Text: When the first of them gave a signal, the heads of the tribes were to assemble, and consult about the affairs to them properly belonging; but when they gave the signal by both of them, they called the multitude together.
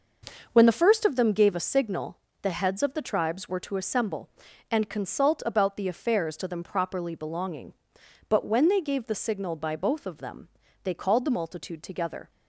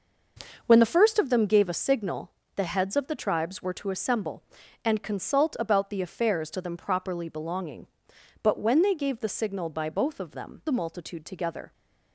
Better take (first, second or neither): first